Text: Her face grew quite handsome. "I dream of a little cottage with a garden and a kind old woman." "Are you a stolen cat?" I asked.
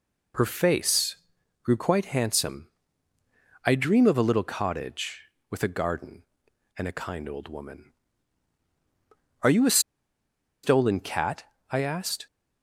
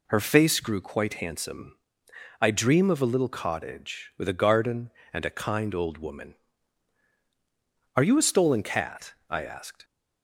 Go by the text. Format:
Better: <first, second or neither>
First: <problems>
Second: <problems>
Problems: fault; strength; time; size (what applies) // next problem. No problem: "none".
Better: second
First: pauses between "face" and "grew"; noticeable; at 1.1 s; 0.48 s long // pauses between "a" and "stolen"; noticeable; at 9.7 s; 0.83 s long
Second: none